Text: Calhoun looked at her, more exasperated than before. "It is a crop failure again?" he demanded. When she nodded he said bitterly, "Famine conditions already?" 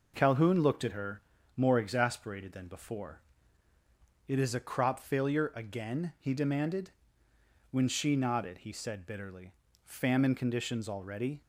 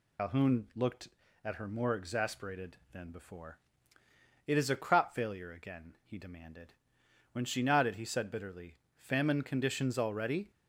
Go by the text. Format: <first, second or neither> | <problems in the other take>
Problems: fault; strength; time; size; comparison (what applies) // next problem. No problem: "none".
first | loses the start of "Calhoun"; at 0.1 s; 95 ms